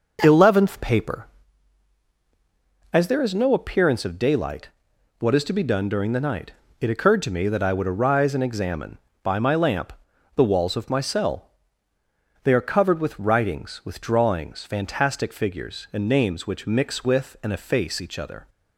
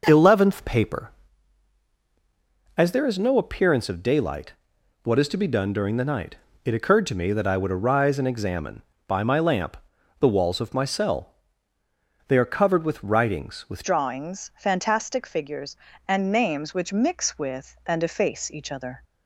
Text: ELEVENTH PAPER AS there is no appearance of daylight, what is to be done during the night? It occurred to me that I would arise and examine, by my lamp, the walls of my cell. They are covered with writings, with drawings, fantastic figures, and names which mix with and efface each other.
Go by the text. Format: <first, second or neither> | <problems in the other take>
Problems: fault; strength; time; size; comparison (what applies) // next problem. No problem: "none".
first | changes voice at "drawings"; from 13.8 s on; 5.2 s long